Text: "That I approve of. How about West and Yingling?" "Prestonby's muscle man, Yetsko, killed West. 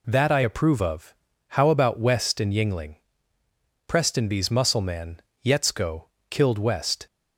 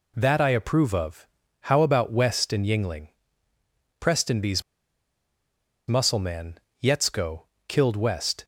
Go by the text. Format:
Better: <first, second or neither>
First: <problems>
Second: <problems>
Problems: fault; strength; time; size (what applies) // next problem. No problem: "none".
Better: first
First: none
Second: pauses between "Prestonby's" and "muscle"; strong; at 4.6 s; 1.2 s long